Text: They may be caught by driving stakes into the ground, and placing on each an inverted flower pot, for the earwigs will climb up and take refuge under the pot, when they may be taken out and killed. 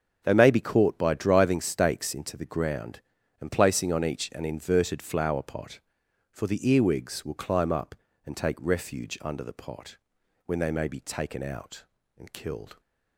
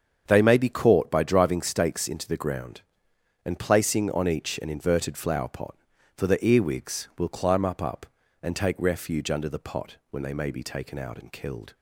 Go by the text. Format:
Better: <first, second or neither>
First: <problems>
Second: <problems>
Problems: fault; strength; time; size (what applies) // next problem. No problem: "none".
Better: first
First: starts louder than the rest; until 1.2 s; 7 dB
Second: starts louder than the rest; strong; until 1.2 s; 7 dB // says "up" twice; at 7.8 s